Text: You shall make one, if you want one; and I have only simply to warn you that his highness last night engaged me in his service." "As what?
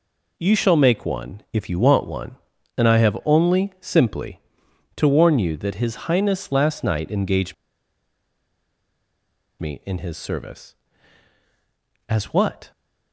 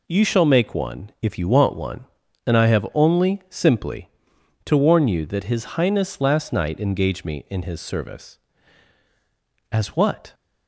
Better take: second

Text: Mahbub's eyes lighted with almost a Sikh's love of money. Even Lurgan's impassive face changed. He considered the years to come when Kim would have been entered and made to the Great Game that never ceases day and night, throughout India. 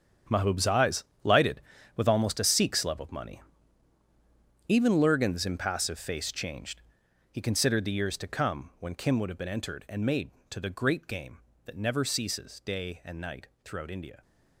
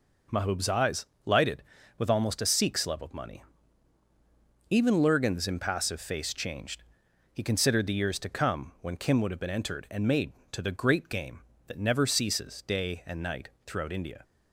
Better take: second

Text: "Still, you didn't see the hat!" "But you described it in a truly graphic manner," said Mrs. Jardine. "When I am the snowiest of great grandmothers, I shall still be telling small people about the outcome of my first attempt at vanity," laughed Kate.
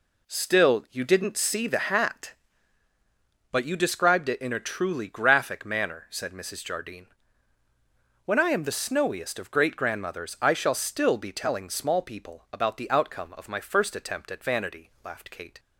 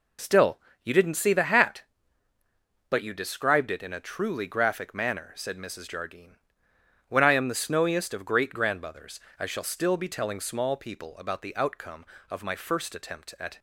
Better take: first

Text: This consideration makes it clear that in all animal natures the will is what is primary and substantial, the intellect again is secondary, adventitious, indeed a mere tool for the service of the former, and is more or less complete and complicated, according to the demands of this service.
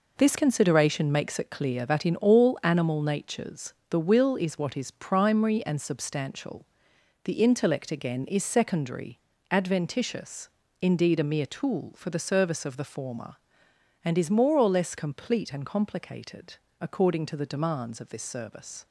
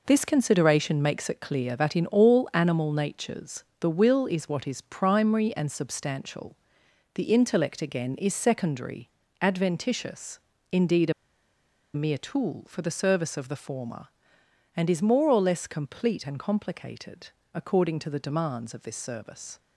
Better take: first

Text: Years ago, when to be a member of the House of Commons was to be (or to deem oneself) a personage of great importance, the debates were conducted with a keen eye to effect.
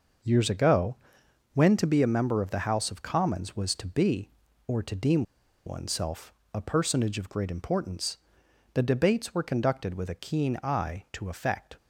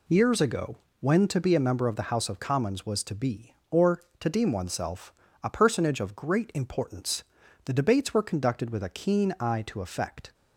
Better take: second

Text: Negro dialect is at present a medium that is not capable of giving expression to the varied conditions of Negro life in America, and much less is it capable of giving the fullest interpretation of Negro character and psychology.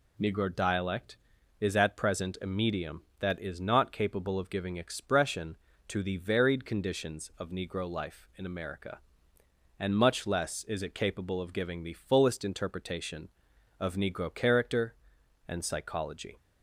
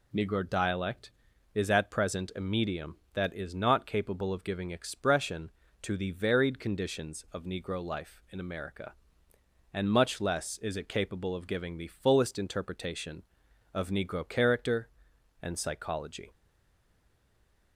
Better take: first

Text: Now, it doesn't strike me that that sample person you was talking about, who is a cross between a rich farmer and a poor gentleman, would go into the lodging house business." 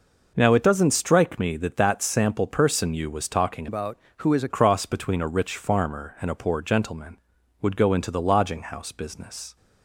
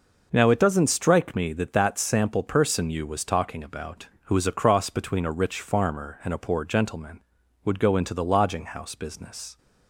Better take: second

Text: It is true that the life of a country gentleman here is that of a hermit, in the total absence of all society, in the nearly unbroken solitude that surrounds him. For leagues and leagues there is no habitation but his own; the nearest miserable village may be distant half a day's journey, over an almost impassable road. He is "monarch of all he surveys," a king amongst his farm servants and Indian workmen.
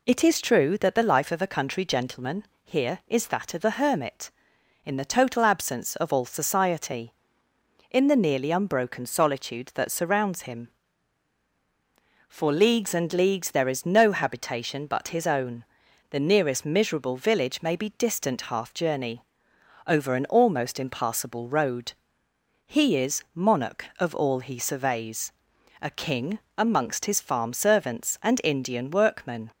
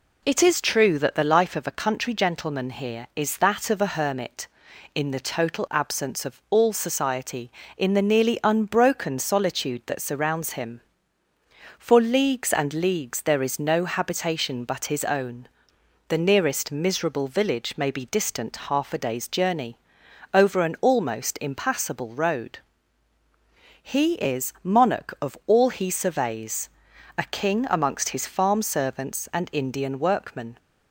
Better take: second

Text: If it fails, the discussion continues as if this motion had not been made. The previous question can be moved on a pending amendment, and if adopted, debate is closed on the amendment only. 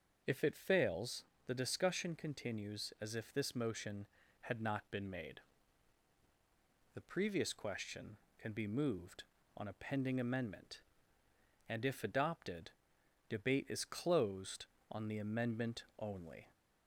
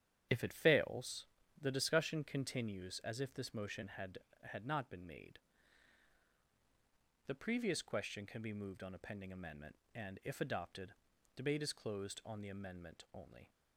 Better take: first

